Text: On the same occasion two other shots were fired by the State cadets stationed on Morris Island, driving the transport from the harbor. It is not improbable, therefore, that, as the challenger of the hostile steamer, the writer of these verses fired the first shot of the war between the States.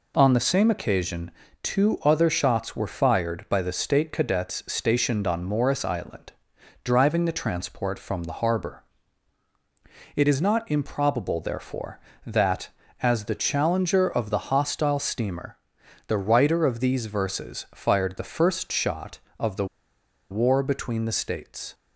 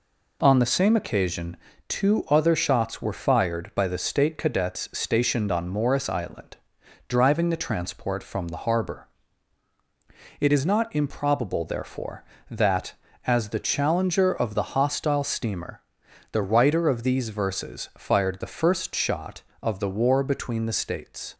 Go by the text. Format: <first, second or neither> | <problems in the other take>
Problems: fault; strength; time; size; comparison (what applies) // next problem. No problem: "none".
second | pauses between "occasion" and "two"; slight; at 1.2 s; 0.32 s long; slight in the second // pauses between "the" and "war"; noticeable; at 19.6 s; 0.65 s long